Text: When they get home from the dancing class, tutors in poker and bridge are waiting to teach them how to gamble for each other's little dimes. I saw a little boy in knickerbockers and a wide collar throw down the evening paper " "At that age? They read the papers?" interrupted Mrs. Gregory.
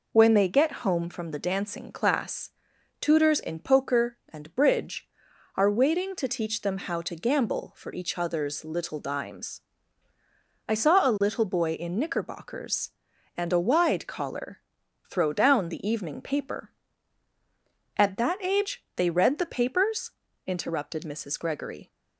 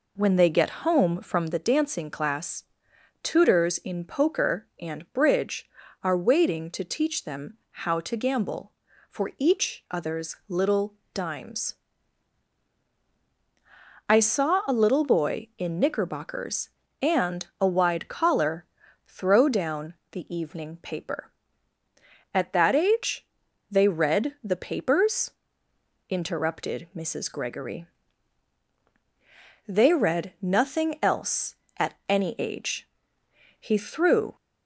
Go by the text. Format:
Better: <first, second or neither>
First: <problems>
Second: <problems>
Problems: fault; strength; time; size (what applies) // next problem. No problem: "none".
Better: first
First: pauses between "collar" and "throw"; noticeable; at 14.6 s; 0.50 s long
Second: pauses between "little" and "dimes"; slight; at 10.9 s; 0.20 s long // pauses between "collar" and "throw"; at 18.6 s; 0.44 s long // pauses between "down" and "the"; slight; at 19.9 s; 0.18 s long // goes on to say "They read nothing else at any age He threw"; strong; from 29.6 s on; 4.6 s long